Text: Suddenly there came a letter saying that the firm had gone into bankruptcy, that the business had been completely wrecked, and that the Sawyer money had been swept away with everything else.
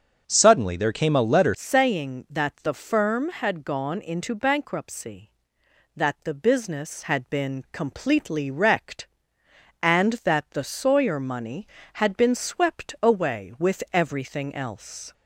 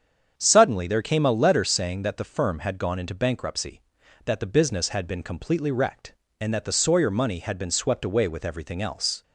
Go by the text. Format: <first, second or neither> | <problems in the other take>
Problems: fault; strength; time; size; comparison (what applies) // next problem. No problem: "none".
second | starts louder than the rest; until 1.2 s; 7 dB; strong in the second // changes voice at "saying"; from 1.5 s on; 13.6 s long